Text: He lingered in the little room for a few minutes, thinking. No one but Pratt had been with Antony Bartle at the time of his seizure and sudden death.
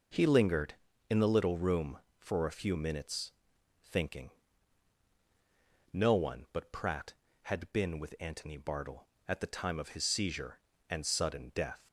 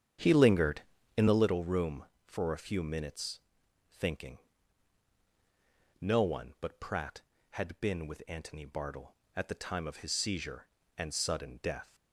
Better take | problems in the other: first | starts louder than the rest; strong; until 1.5 s; 8.5 dB

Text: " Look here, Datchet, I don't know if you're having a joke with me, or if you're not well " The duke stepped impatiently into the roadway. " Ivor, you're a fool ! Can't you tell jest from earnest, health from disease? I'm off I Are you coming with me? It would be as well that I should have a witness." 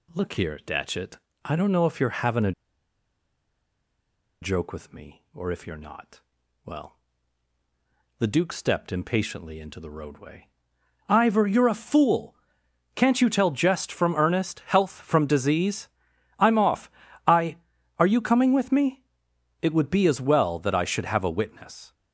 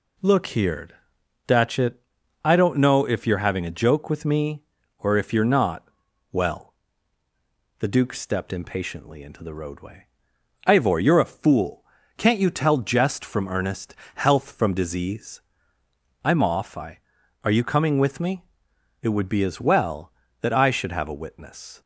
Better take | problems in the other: second | pauses between "a" and "joke"; strong; at 2.5 s; 1.9 s long // pauses between "not" and "well"; at 6.2 s; 0.42 s long; also in the second // pauses between "off" and "I"; slight; at 16.9 s; 0.34 s long

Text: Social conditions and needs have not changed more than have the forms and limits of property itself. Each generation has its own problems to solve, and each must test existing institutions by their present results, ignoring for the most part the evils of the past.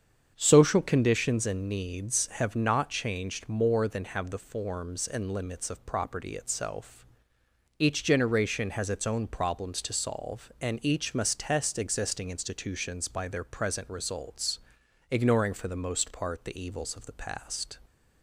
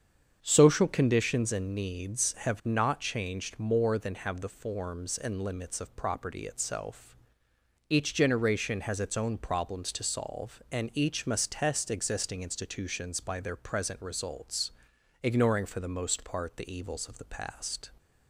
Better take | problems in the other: neither | starts louder than the rest; strong; the same in both

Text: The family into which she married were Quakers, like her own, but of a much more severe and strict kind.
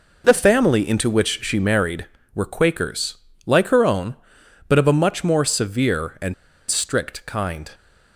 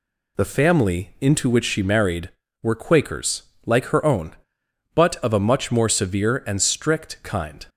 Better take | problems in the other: second | pauses between "and" and "strict"; slight; at 6.3 s; 0.35 s long

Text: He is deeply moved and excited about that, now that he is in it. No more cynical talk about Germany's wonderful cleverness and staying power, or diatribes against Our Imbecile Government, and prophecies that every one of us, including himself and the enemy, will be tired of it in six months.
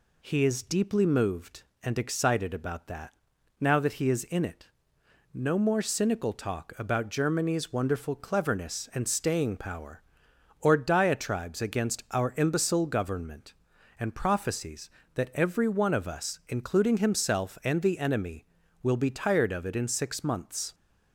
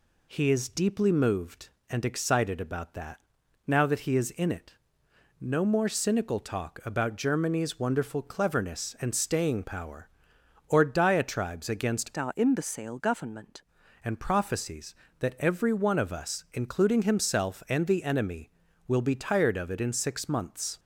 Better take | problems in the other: first | changes voice from "Our" to "Government"; from 12.1 to 13.6 s; 1.5 s long

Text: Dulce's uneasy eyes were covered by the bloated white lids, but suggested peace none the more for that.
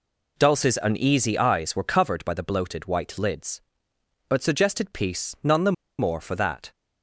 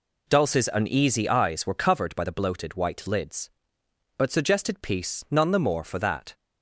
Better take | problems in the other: second | pauses between "the" and "more"; slight; at 5.7 s; 0.26 s long

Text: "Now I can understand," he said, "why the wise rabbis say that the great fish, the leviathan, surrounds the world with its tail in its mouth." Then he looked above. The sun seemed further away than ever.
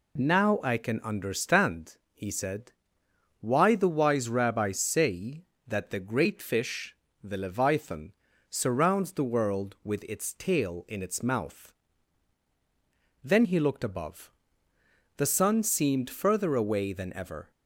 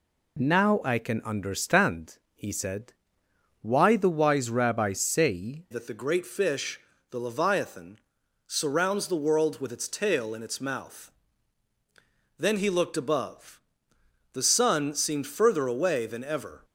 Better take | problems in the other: first | changes voice at "that"; from 5.7 s on; 10.9 s long

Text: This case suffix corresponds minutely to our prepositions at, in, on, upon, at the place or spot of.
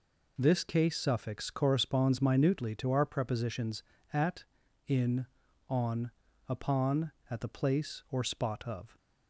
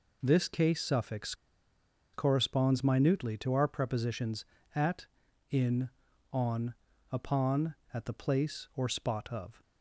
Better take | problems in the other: first | pauses between "suffix" and "corresponds"; noticeable; at 1.3 s; 0.79 s long

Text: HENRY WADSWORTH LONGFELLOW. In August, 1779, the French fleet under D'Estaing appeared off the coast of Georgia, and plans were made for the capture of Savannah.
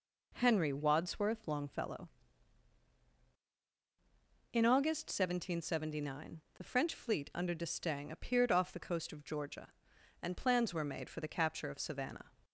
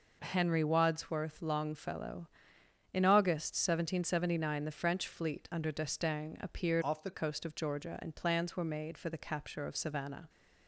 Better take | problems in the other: first | changes voice from "off" to "the"; from 6.8 to 7.1 s; 0.3 s long

